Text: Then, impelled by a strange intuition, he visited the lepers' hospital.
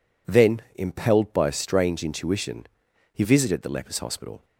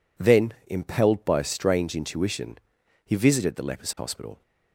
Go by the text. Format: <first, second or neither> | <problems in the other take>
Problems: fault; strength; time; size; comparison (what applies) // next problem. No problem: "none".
neither | none